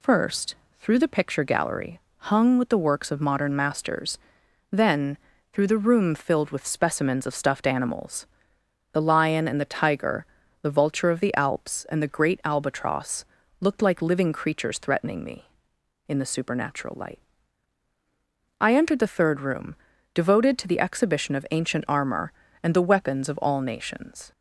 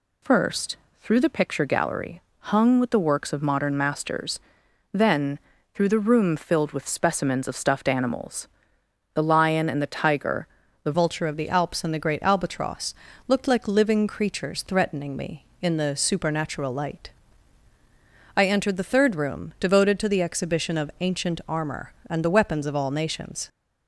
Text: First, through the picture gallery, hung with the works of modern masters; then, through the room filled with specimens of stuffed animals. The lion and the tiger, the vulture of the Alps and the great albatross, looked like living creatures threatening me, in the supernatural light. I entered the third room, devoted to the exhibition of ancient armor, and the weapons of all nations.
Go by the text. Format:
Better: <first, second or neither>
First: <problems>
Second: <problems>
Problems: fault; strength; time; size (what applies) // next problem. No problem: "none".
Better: first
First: none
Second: changes voice at "vulture"; from 10.9 s on; 12.5 s long